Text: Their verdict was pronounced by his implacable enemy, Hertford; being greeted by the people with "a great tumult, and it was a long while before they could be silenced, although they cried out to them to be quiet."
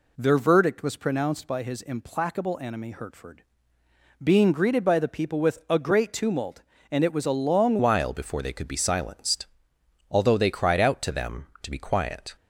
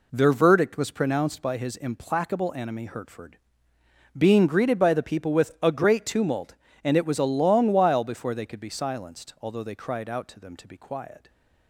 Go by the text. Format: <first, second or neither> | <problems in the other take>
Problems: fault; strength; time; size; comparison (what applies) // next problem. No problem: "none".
second | changes voice at "while"; from 7.7 s on; 4.6 s long